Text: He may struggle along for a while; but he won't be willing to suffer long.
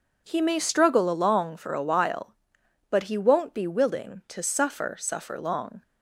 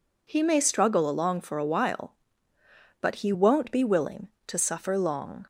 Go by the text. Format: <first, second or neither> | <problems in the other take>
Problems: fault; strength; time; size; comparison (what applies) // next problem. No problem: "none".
second | says "suffer" twice; at 4.9 s